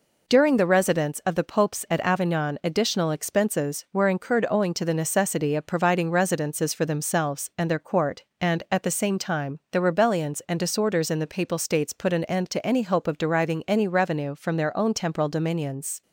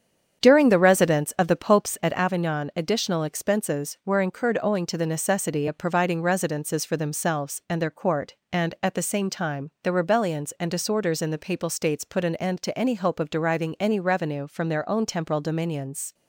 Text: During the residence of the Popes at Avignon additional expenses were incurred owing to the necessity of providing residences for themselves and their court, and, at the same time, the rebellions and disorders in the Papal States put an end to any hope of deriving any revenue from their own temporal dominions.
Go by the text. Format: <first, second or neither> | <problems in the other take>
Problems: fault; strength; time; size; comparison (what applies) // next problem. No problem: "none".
first | starts louder than the rest; strong; until 2.2 s; 8 dB